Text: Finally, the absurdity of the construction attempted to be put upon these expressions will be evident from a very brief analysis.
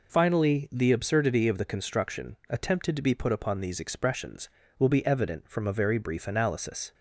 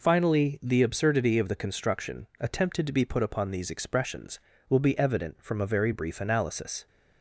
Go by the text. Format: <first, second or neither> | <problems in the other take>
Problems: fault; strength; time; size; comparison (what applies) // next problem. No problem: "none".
neither | none